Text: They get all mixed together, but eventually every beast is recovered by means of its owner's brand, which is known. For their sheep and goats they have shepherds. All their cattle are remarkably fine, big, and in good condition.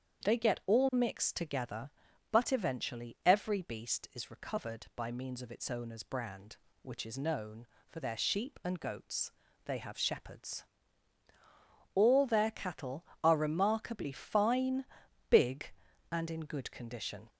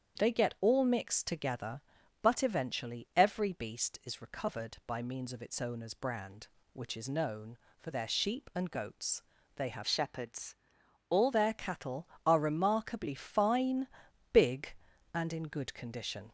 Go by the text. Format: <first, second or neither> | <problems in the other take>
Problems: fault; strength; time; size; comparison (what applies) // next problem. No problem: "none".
first | starts louder than the rest; strong; until 1.2 s; 8 dB; strong in the first // pauses between "goats" and "they"; slight; at 9.2 s; 0.36 s long; slight in the first // changes voice from "shepherds" to "All"; from 9.8 to 11.2 s; 1.4 s long